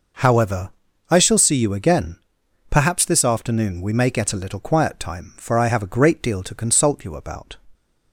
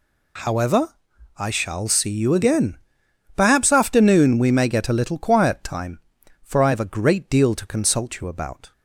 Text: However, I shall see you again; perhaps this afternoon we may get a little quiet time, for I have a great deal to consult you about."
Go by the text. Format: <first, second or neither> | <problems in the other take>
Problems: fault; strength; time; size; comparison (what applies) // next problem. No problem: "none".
first | skips "this"; at 3.7 s